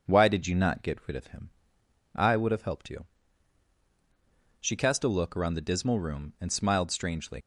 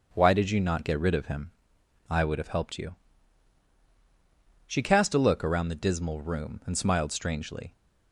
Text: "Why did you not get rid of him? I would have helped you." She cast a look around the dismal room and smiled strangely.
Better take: second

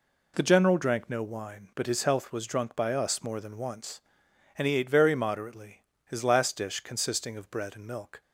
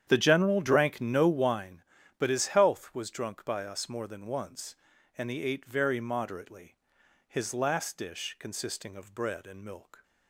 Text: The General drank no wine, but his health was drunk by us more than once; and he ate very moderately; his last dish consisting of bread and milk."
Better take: first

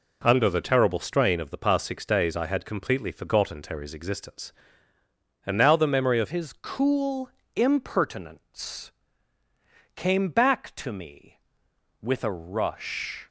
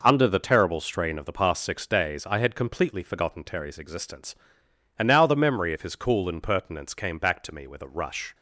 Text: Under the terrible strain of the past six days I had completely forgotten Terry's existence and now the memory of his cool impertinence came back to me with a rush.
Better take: second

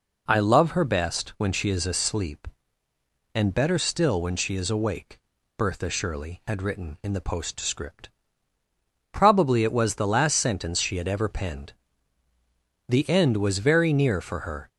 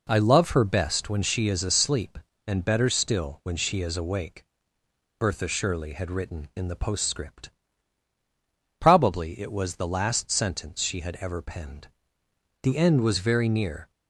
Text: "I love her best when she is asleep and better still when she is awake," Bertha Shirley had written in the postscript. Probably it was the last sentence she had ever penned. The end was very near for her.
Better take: first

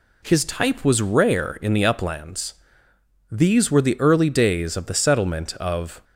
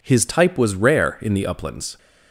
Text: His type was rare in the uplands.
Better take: second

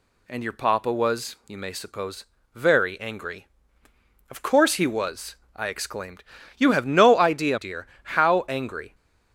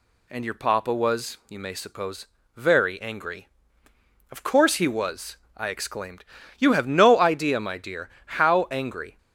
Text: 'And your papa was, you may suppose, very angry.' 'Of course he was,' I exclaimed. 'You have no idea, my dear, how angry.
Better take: second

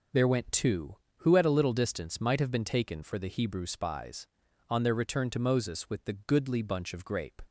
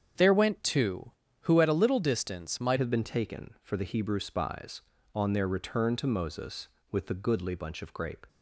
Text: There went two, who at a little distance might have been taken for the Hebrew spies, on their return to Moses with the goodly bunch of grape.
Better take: first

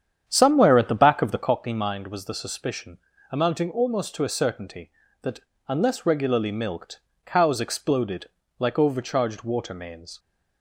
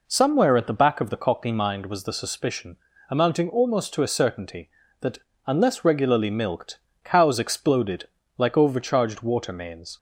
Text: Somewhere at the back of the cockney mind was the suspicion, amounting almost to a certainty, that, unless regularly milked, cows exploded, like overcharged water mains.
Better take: second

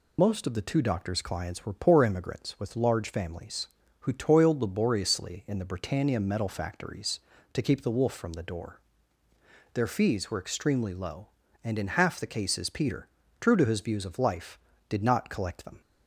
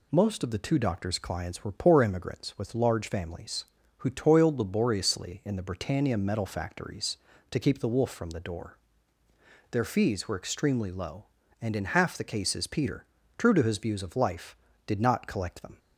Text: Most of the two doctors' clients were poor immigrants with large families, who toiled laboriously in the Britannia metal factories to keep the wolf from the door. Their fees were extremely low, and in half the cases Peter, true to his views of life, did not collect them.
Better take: second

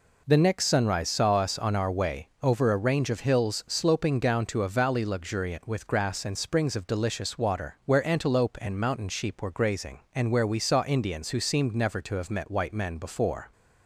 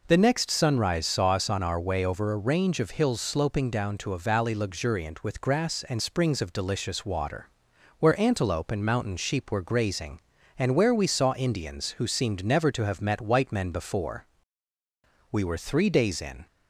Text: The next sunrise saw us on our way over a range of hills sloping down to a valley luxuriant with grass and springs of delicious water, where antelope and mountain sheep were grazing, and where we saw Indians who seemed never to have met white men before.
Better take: first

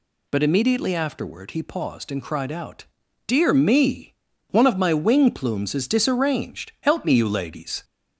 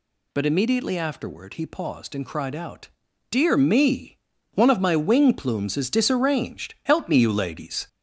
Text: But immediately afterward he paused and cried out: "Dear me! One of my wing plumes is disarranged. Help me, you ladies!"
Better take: first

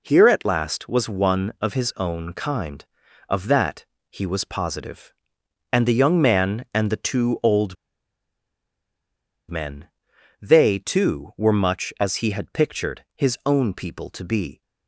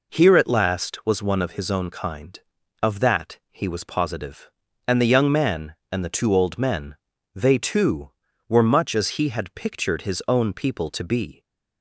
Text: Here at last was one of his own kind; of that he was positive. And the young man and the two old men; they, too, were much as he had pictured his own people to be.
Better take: second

